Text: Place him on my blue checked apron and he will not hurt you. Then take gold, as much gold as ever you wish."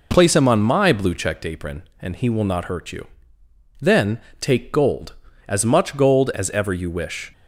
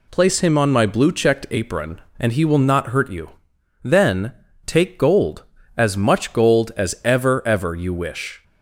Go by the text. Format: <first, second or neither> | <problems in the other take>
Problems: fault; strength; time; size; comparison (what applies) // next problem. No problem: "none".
first | pauses between "Then" and "take"; slight; at 4.3 s; 0.32 s long; slight in the first // says "ever" twice; at 7.4 s